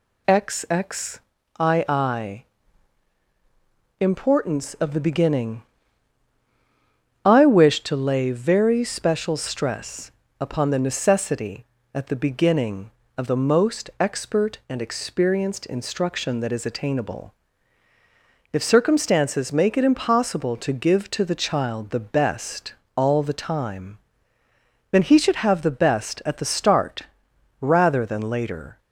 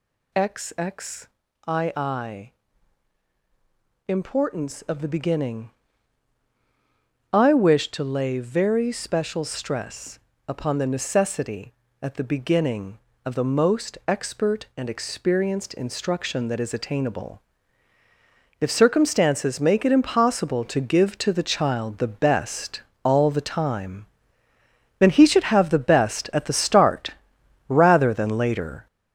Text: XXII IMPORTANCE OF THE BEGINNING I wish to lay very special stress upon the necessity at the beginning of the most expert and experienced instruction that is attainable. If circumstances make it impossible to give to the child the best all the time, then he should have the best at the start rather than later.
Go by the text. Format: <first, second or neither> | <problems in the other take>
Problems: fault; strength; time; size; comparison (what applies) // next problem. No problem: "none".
first | gets louder; strong; throughout; 10.5 dB // pauses between "XXII" and "IMPORTANCE"; strong; at 1.9 s; 2.1 s long; strong in the first // pauses between "BEGINNING" and "I"; strong; at 5.6 s; 1.6 s long; strong in the first // pauses between "stress" and "upon"; slight; at 10.1 s; 0.30 s long; slight in the first // pauses between "best" and "all"; slight; at 22.8 s; 0.24 s long; slight in the first // pauses between "start" and "rather"; noticeable; at 27.1 s; 0.58 s long; noticeable in the first